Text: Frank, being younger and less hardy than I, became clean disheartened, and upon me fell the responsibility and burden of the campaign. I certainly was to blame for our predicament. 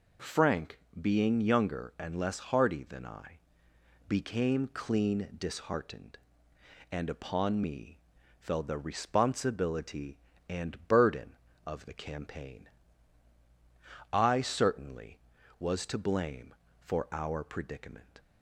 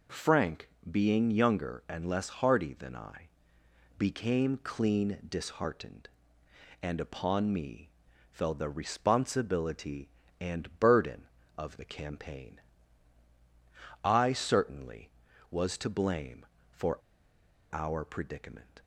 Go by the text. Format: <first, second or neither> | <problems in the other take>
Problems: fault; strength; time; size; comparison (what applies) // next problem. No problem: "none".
first | pauses between "me" and "fell"; at 7.9 s; 0.42 s long; also in the first // pauses between "for" and "our"; noticeable; at 16.9 s; 0.75 s long